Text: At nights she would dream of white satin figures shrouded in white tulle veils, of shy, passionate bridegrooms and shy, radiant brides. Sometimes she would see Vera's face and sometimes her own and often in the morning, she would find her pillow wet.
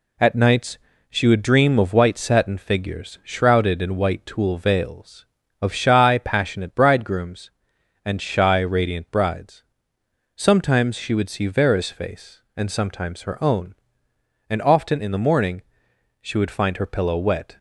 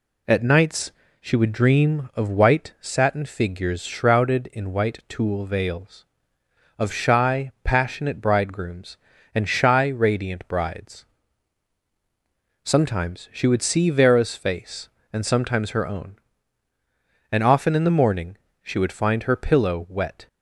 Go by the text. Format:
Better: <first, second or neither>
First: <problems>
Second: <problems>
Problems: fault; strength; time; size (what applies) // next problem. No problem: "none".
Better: neither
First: pauses between "nights" and "she"; slight; at 0.7 s; 0.32 s long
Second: pauses between "nights" and "she"; slight; at 0.9 s; 0.30 s long